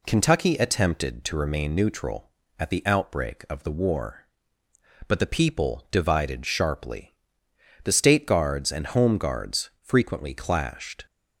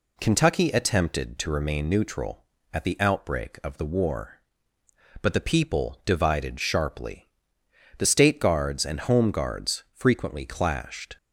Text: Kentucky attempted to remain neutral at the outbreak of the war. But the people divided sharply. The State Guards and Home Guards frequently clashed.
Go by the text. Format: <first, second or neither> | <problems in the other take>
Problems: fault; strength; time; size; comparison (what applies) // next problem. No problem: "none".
neither | none